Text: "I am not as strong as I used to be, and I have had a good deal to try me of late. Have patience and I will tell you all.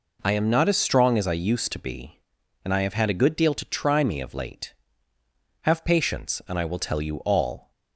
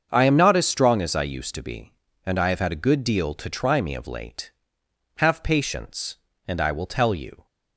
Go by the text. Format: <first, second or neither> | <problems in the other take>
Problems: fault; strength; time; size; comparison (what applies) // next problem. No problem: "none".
first | starts louder than the rest; until 1.1 s; 7 dB // stops before "all"; at 7.4 s